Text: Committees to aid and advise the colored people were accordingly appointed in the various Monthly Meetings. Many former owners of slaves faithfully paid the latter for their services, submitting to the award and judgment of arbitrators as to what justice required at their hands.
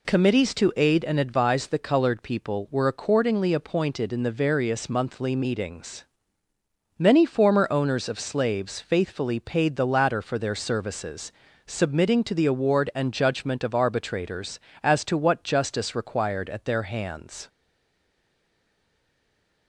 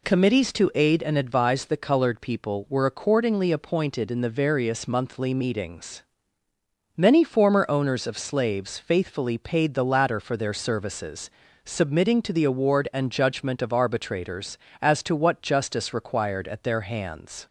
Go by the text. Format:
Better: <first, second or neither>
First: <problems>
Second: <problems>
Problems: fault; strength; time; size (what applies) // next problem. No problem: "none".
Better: second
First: stays silent after the last word; from 17.4 s on; 2.2 s long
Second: none